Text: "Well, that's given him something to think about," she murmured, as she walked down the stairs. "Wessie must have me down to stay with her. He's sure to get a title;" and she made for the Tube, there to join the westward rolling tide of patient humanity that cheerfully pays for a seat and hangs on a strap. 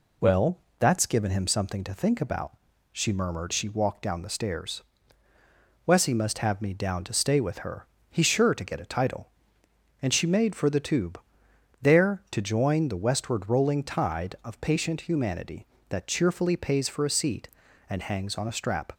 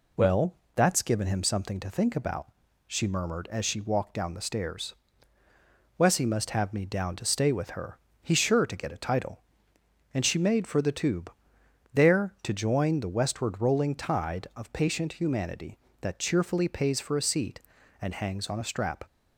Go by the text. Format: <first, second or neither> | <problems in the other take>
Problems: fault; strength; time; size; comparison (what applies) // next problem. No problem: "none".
second | skips "as"; at 3.5 s